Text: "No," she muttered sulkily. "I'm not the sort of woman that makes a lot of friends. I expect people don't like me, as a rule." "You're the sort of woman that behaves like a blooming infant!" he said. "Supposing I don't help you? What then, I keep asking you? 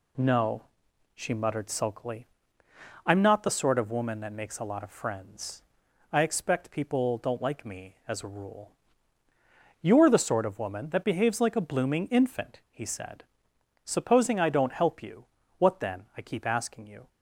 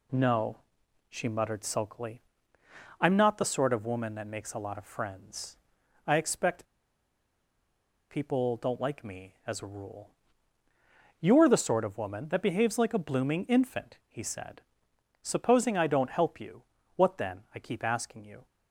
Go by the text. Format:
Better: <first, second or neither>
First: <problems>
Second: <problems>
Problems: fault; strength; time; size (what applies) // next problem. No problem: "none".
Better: first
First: none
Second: pauses between "expect" and "people"; strong; at 6.6 s; 1.4 s long